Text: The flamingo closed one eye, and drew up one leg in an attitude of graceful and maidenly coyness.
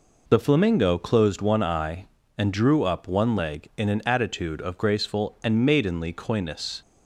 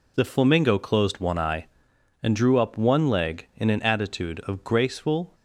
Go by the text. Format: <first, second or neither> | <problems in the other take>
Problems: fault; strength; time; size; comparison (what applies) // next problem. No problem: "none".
first | stops before "and maidenly coyness"; at 5.3 s